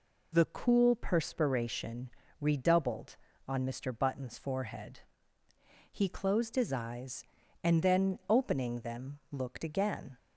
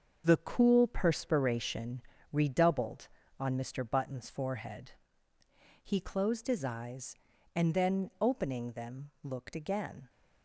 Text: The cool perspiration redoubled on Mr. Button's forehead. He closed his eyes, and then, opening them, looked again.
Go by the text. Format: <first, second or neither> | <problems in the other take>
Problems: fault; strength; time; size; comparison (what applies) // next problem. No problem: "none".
first | gets quieter; strong; throughout; 8 dB // pauses between "perspiration" and "redoubled"; slight; at 2.0 s; 0.30 s long; slight in the first